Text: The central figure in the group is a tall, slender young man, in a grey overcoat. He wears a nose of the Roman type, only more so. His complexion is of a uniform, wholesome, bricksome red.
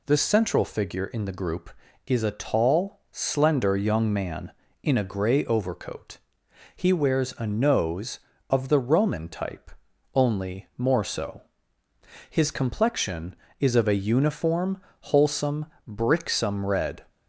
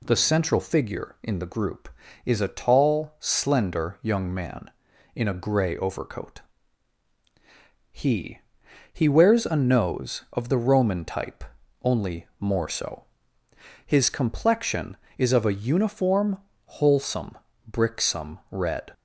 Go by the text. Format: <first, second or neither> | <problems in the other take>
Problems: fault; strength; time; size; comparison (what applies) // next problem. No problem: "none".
first | says "He" twice; at 8.9 s